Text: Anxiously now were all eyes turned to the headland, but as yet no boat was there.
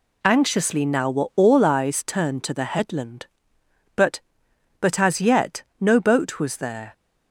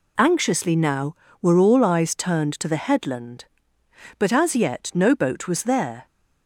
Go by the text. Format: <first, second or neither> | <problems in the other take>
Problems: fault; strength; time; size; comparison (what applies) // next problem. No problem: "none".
second | says "but" twice; at 4.7 s // pauses between "yet" and "no"; slight; at 5.6 s; 0.16 s long